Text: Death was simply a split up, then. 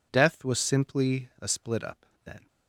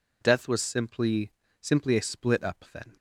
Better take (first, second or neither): first